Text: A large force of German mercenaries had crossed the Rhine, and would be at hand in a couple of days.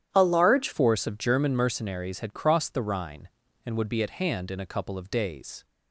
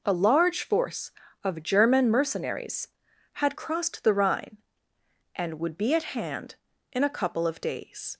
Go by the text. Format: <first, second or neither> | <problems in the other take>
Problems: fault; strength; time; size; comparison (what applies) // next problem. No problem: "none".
second | starts louder than the rest; strong; until 1.1 s; 10.5 dB // changes voice at "force"; from 0.7 s on; 4.9 s long